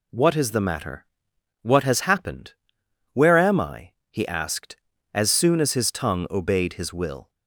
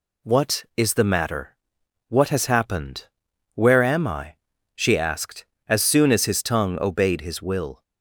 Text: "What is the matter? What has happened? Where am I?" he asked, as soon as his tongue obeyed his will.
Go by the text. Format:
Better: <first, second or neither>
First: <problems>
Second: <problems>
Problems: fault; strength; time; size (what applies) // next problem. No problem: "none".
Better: first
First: none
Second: says "she" for "he"; at 4.7 s